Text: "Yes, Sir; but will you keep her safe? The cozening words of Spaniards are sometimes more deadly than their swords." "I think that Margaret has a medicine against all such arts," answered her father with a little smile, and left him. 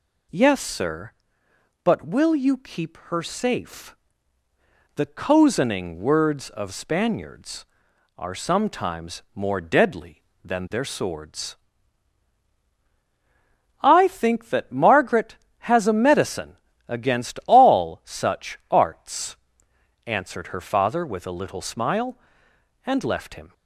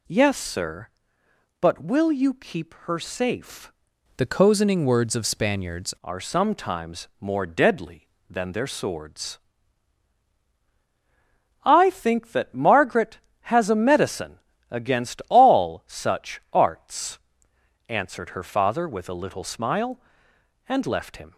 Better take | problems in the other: first | changes voice from "The" to "Spaniards"; from 4.1 to 5.9 s; 1.8 s long // pauses between "medicine" and "against"; slight; at 14.3 s; 0.30 s long; slight in the first

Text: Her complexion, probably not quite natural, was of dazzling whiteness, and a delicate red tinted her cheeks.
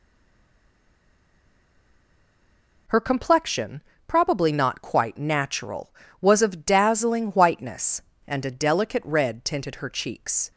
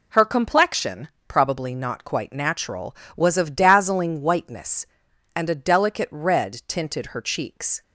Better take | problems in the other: second | stays silent before the first word; strong; until 2.8 s; 2.8 s long

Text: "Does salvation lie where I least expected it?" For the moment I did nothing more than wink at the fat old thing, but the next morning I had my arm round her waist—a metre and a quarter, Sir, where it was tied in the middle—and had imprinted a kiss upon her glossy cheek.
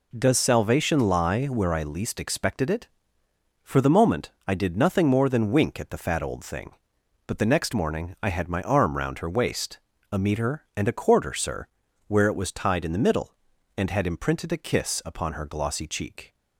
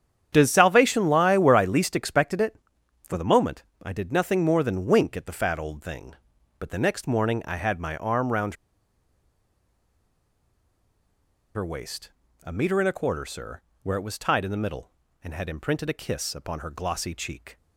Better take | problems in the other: first | starts louder than the rest; strong; until 1.3 s; 9 dB // pauses between "moment" and "I"; slight; at 3.6 s; 0.22 s long; slight in the first // pauses between "round" and "her"; strong; at 8.5 s; 2.9 s long

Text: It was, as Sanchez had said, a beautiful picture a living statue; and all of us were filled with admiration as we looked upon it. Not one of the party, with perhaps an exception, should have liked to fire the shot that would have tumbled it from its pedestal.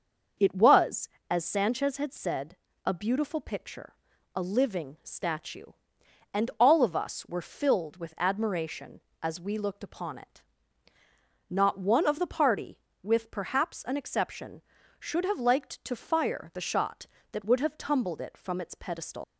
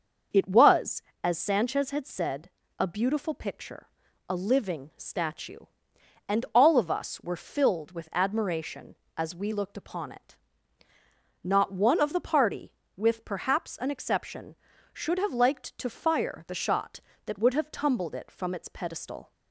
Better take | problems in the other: second | starts louder than the rest; until 1.5 s; 6.5 dB; also in the second // pauses between "picture" and "a"; at 3.9 s; 0.40 s long; also in the second // leaves "pedestal" unfinished; at 19.2 s; 130 ms

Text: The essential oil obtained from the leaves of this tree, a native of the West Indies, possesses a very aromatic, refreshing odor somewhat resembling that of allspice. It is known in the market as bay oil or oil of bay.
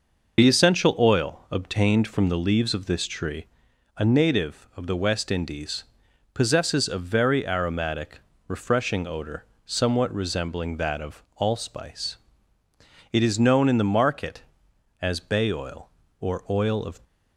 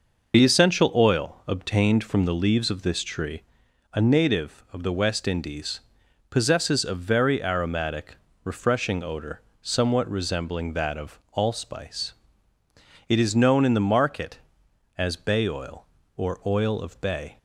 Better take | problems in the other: second | pauses between "odor" and "somewhat"; slight; at 9.4 s; 0.22 s long; slight in the second // stops before "bay"; at 17.0 s

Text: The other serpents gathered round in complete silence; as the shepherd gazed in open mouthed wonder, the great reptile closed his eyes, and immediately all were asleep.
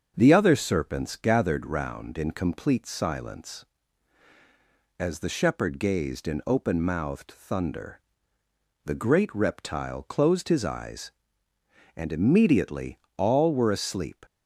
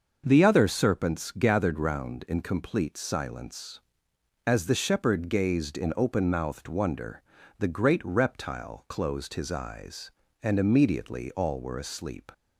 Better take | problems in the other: second | starts louder than the rest; until 1.1 s; 6.5 dB; also in the second // says "thunder" for "wonder"; at 7.3 s // pauses between "immediately" and "all"; slight; at 12.9 s; 0.22 s long

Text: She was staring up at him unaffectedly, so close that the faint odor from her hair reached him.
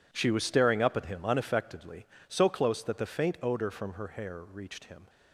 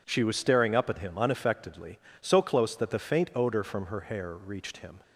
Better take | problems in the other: second | gets quieter; strong; throughout; 15 dB

